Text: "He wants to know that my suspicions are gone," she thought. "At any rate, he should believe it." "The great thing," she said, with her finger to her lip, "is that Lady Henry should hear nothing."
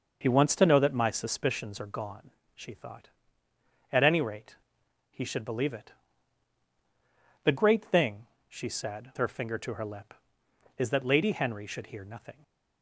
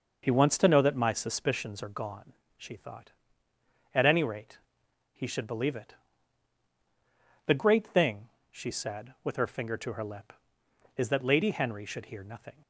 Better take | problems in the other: second | starts louder than the rest; noticeable; until 1.2 s; 6 dB; noticeable in the second // skips "with"; at 9.1 s

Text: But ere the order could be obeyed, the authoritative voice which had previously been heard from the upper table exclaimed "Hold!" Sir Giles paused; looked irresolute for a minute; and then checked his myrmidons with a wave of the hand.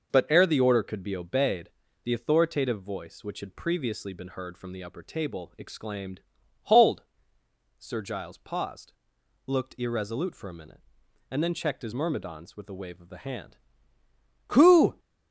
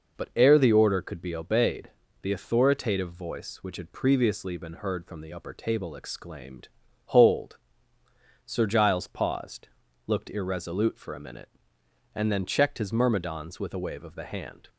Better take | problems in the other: second | pauses between "exclaimed" and "Hold"; at 6.2 s; 0.42 s long; also in the second // goes on to say "Who"; from 14.4 s on; 0.52 s long

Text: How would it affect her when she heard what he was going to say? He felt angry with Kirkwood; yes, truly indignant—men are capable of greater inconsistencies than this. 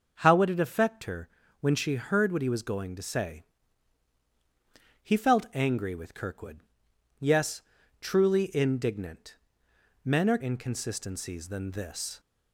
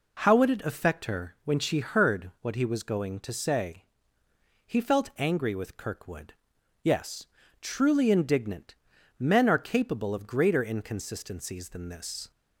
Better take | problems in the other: second | starts louder than the rest; noticeable; until 1.1 s; 6 dB // pauses between "her" and "when"; slight; at 1.2 s; 0.32 s long // skips "capable of greater"; at 10.3 s

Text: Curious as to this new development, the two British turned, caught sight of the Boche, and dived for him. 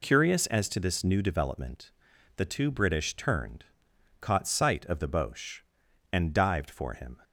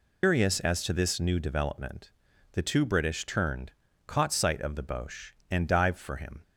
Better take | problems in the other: first | loses the start of "Curious"; at 0.2 s; 160 ms

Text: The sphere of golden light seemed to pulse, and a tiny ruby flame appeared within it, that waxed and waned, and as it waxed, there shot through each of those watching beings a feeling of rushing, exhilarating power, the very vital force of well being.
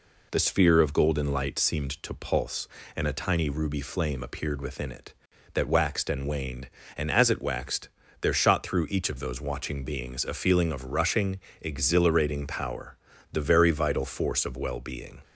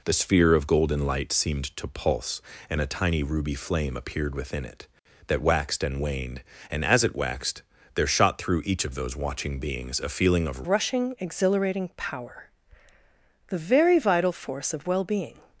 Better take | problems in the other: first | changes voice at "rushing"; from 10.6 s on; 4.7 s long

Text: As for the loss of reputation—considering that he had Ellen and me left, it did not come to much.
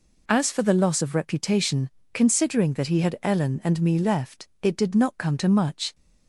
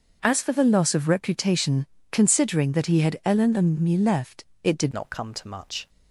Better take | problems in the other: first | starts louder than the rest; until 1.2 s; 6 dB // changes voice at "not"; from 4.9 s on; 0.9 s long

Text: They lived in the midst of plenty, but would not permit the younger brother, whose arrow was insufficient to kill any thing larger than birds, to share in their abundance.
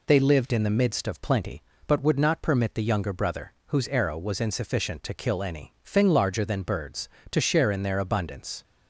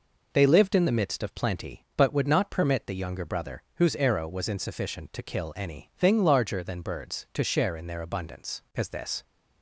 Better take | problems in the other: first | goes on to say "As this"; slight; from 8.7 s on; 0.48 s long

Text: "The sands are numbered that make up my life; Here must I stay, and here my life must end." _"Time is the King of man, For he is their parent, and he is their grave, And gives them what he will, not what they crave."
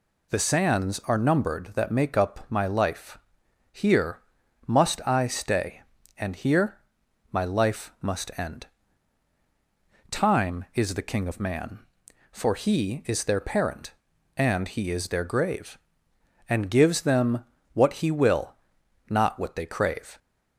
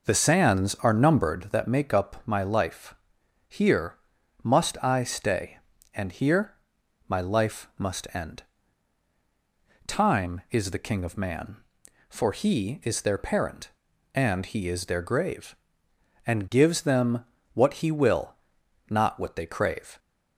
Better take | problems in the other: first | starts louder than the rest; noticeable; until 1.7 s; 5.5 dB // pauses between "Here" and "must"; noticeable; at 3.9 s; 0.46 s long; noticeable in the first // pauses between "here" and "my"; noticeable; at 6.5 s; 0.50 s long; noticeable in the first // pauses between "them" and "what"; slight; at 17.2 s; 0.28 s long; slight in the first

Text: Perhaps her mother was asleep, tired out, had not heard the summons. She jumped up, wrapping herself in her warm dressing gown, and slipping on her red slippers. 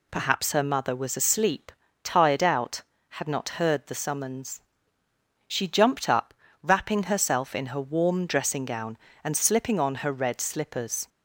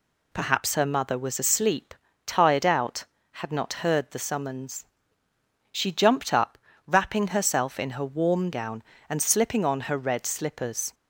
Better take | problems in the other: first | skips "dressing"; at 8.5 s

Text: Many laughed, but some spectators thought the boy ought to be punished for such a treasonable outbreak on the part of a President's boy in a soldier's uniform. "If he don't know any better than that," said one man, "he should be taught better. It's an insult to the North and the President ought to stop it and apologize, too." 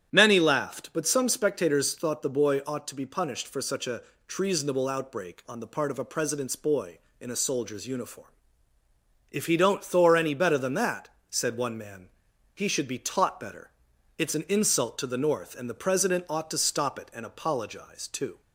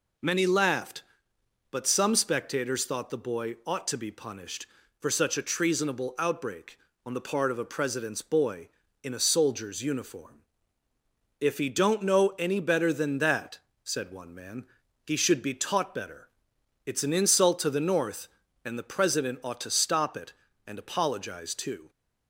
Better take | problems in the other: second | starts louder than the rest; strong; until 1.1 s; 9 dB // pauses between "a" and "treasonable"; slight; at 4.0 s; 0.24 s long // says "thor" for "know"; at 9.8 s

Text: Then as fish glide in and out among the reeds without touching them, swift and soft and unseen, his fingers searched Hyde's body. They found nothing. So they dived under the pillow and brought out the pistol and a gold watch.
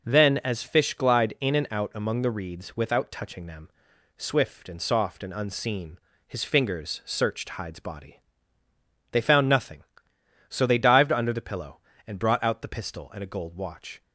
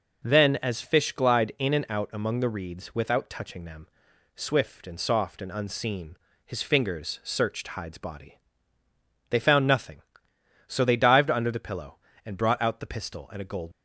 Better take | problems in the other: first | stops before "watch"; at 13.7 s

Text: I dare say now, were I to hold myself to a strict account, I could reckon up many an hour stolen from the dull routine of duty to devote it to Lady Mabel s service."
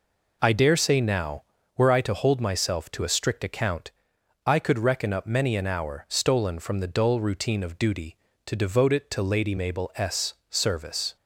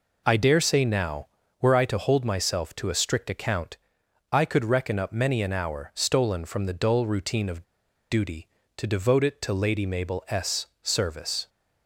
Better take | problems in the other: first | pauses between "of" and "duty"; at 7.6 s; 0.45 s long // pauses between "s" and "service"; slight; at 10.6 s; 0.16 s long; slight in the first

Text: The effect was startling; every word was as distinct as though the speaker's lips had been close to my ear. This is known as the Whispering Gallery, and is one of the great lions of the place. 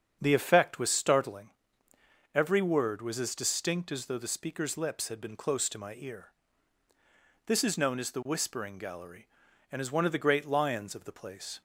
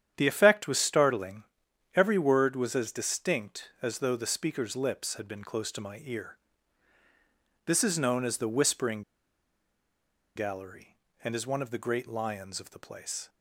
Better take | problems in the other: first | starts louder than the rest; strong; until 1.1 s; 9.5 dB; strong in the first // pauses between "Whispering" and "Gallery"; strong; at 9.0 s; 1.3 s long

